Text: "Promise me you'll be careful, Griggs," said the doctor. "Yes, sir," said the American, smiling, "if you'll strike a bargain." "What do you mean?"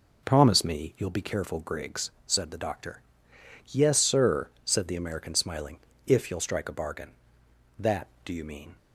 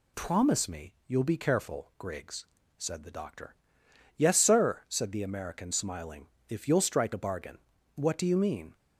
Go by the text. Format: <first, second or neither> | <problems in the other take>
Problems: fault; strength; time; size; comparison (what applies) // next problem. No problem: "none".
second | says "That" for "What"; at 7.7 s